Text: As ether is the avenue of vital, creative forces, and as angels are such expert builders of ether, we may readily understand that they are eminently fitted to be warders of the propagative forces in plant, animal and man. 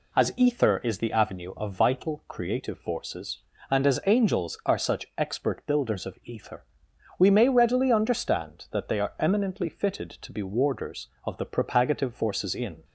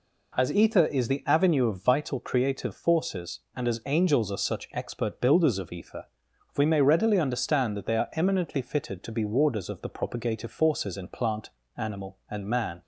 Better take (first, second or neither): second